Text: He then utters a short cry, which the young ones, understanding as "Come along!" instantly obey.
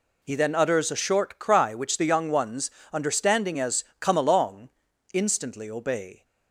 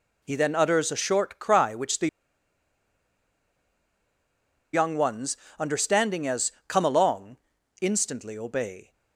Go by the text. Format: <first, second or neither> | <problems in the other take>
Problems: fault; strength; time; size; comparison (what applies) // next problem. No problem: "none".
first | pauses between "the" and "young"; strong; at 2.0 s; 2.6 s long // pauses between "as" and "Come"; slight; at 6.5 s; 0.16 s long; slight in the first